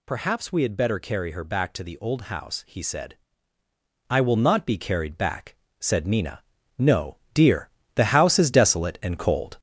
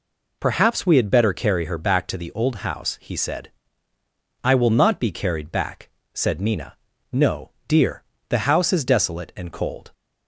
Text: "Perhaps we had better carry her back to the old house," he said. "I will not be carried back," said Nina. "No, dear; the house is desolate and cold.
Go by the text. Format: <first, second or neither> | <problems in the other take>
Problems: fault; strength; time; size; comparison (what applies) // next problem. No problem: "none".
second | gets louder; noticeable; throughout; 5 dB